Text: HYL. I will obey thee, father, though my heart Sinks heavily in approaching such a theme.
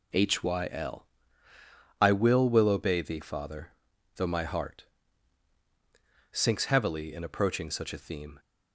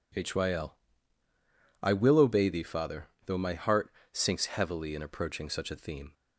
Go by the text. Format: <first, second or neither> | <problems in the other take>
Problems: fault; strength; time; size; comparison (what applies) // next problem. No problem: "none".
second | says "will" twice; at 2.4 s // pauses between "heart" and "Sinks"; strong; at 4.8 s; 1.4 s long; slight in the second